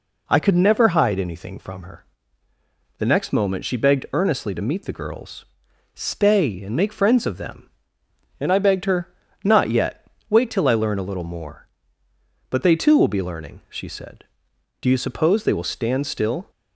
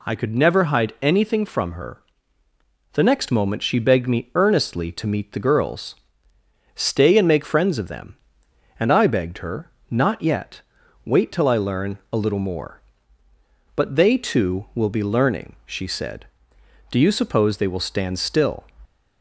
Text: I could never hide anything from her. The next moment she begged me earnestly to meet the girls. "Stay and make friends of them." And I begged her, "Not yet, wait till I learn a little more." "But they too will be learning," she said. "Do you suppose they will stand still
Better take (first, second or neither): second